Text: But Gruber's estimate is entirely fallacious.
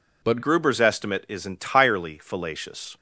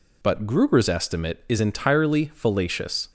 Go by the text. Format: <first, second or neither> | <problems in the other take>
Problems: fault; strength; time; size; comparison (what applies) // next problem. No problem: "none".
second | changes voice at "Gruber's"; from 0.4 s on; 2.5 s long